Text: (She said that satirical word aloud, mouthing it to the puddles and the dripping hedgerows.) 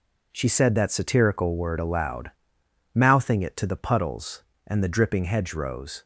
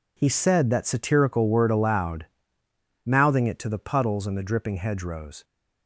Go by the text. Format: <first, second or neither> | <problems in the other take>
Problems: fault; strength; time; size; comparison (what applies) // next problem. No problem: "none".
first | says "He" for "She"; at 0.1 s